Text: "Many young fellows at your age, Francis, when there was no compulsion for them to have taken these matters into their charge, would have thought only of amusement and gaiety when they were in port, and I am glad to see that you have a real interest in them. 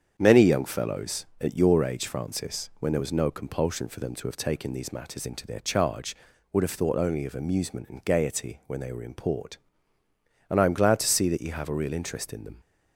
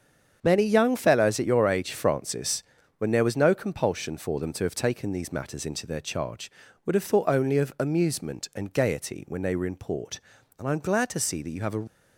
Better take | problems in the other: first | starts louder than the rest; strong; until 1.4 s; 7.5 dB; strong in the first // stops before "real interest in them"; at 11.8 s

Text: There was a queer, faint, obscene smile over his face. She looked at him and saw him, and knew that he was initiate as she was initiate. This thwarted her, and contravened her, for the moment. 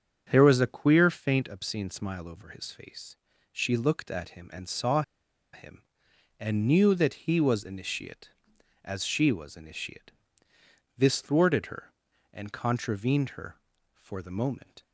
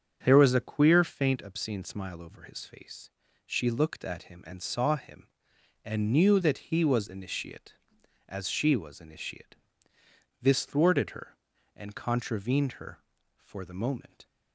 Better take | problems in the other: second | starts louder than the rest; strong; until 1.3 s; 7 dB; strong in the second // pauses between "saw" and "him"; noticeable; at 5.0 s; 0.51 s long

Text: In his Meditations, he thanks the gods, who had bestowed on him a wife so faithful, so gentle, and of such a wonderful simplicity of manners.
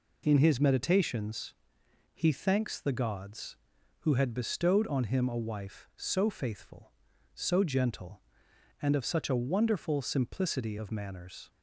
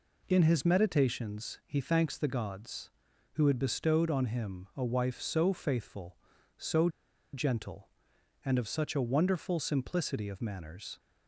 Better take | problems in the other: first | pauses between "so" and "gentle"; at 6.8 s; 0.45 s long

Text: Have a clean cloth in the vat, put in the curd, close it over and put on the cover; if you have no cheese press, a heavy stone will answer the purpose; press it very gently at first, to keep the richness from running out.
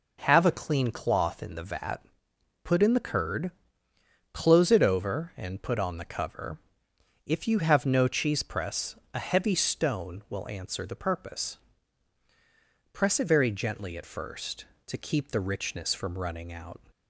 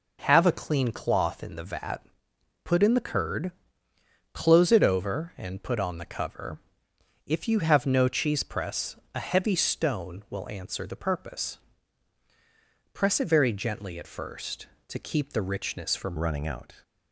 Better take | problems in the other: first | changes voice at "running"; from 16.1 s on; 0.7 s long

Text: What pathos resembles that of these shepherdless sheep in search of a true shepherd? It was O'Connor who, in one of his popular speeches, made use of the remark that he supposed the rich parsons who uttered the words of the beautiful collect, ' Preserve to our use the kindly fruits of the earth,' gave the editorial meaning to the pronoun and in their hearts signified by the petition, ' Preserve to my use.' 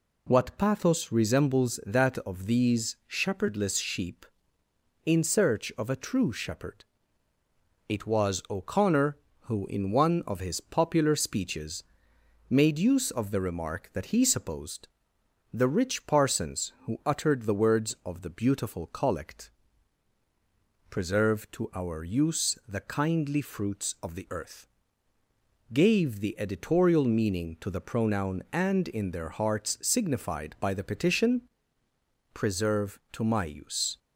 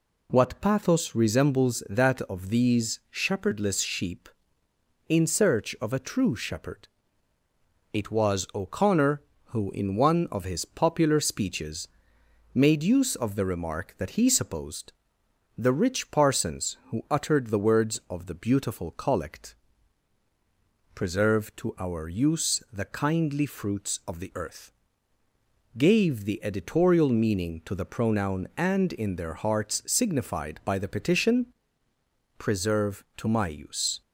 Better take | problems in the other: neither | pauses between "supposed" and "the"; noticeable; the same in both

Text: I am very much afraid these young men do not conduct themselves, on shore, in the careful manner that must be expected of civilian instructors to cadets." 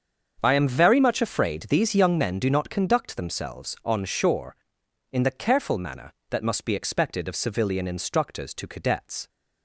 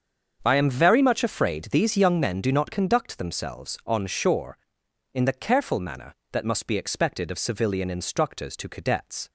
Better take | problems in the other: neither | starts louder than the rest; the same in both

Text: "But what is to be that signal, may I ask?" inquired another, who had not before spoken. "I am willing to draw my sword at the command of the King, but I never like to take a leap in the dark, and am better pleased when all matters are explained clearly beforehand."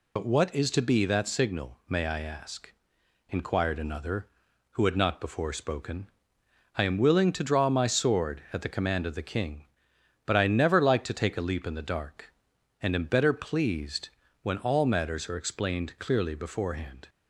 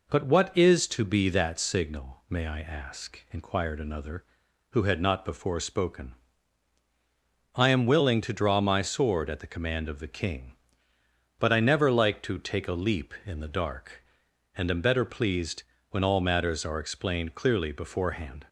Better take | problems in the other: second | loses the start of "But"; at 0.1 s; 80 ms // pauses between "pleased" and "when"; slight; at 14.0 s; 0.34 s long; slight in the second

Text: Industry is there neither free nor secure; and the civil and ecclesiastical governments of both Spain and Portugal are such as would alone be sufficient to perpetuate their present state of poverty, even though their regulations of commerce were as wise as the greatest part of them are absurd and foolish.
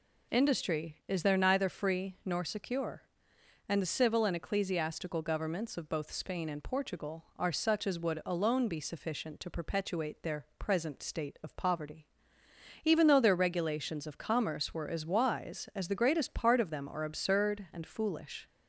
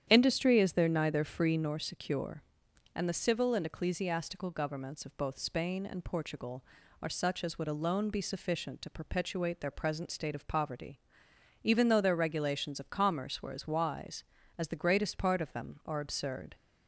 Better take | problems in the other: first | starts louder than the rest; strong; until 1.1 s; 9.5 dB // stops before "and foolish"; at 16.5 s

